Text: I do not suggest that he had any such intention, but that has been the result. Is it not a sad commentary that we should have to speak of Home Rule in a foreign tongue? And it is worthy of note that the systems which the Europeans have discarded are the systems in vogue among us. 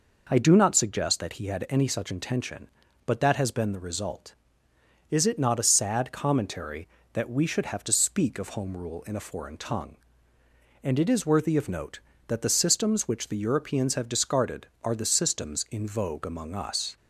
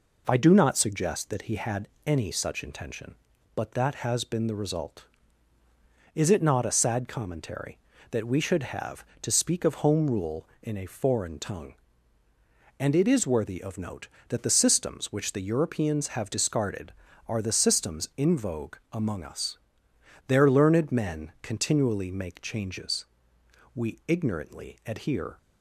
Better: first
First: none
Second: pauses between "had" and "any"; slight; at 1.8 s; 0.18 s long // pauses between "vogue" and "among"; slight; at 18.7 s; 0.16 s long // goes on to say "Their learned men continually make changes We ignorantly adhere"; strong; from 20.2 s on; 5.1 s long

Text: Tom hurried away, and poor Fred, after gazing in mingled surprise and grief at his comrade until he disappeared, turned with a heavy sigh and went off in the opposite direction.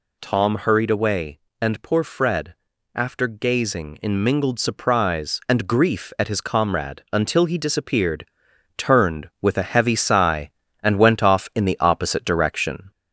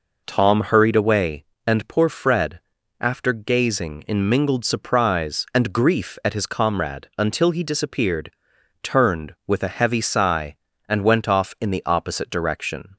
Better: second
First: gets louder; slight; throughout; 2.5 dB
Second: none

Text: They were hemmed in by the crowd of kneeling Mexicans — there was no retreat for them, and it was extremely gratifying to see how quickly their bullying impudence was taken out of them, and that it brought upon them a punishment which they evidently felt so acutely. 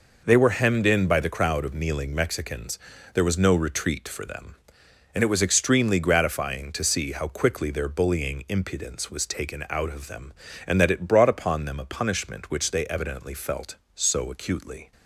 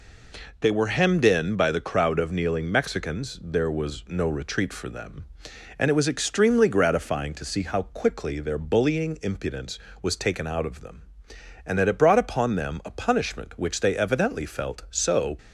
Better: first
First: none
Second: stops before "acutely"; at 15.3 s

